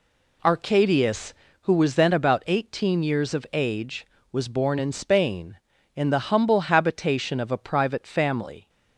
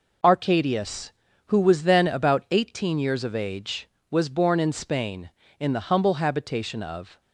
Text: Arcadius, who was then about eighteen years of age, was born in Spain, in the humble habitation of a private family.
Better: first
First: none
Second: stops before "a private family"; at 7.2 s

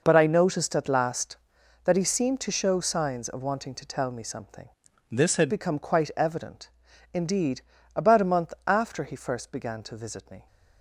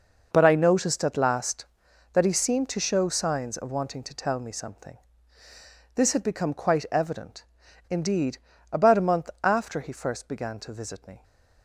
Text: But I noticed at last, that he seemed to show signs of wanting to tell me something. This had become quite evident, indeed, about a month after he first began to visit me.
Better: second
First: changes voice from "This" to "had"; from 5.1 to 5.4 s; 0.3 s long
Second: none

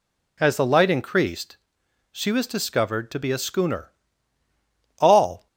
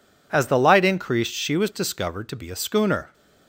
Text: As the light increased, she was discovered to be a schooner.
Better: second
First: goes on to say "All"; slight; from 4.9 s on; 0.48 s long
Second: none

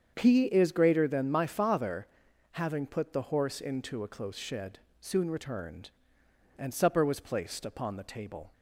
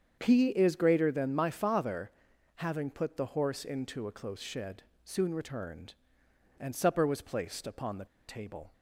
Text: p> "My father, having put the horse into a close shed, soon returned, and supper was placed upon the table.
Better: first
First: starts louder than the rest; strong; until 1.1 s; 7.5 dB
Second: starts louder than the rest; strong; until 1.2 s; 7.5 dB // pauses between "the" and "table"; slight; at 8.0 s; 0.21 s long

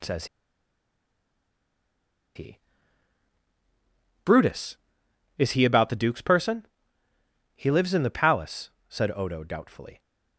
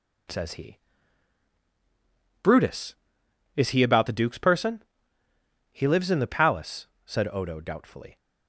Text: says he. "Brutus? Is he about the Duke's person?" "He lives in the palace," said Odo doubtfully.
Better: second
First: pauses between "says" and "he"; strong; at 0.2 s; 2.0 s long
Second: none

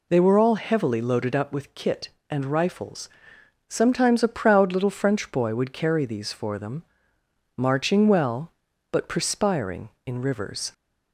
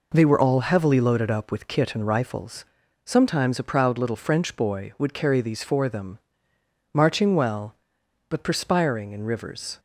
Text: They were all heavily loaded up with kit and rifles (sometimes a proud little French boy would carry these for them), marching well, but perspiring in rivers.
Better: neither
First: none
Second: none

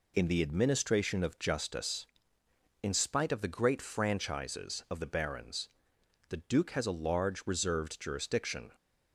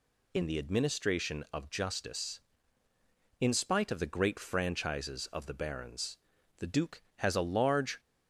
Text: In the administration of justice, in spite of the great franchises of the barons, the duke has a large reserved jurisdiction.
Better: first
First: none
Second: stops before "reserved jurisdiction"; at 7.9 s

